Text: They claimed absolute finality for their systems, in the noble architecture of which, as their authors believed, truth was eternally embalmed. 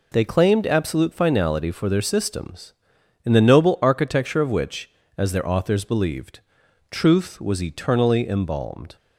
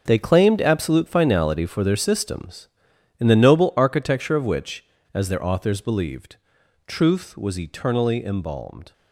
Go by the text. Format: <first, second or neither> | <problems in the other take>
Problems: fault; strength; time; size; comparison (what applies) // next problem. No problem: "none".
first | gets quieter; strong; throughout; 11 dB